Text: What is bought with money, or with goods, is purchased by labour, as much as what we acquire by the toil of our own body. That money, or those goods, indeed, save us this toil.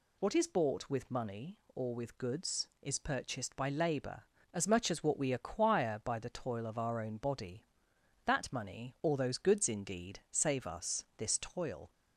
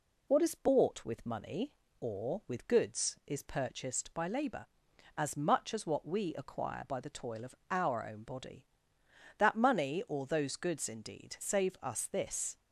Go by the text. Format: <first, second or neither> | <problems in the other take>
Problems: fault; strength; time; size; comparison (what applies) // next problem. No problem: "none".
first | pauses between "of" and "our"; slight; at 7.5 s; 0.16 s long // stops before "toil"; at 12.5 s